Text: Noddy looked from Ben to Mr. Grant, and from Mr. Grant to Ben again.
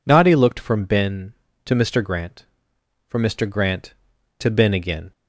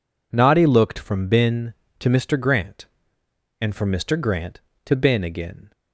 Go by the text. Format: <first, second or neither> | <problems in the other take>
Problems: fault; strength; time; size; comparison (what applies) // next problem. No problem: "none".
second | skips "and"; at 2.7 s